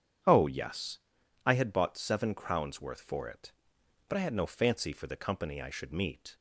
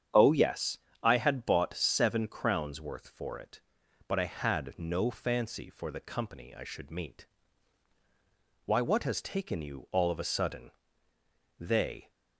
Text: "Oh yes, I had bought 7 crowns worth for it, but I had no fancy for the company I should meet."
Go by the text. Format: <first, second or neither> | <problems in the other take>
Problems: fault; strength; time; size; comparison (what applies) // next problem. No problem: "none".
first | starts louder than the rest; strong; until 1.3 s; 8.5 dB; strong in the first // goes on to say "Why what has taken you all of a sudden They"; strong; from 8.6 s on; 3.4 s long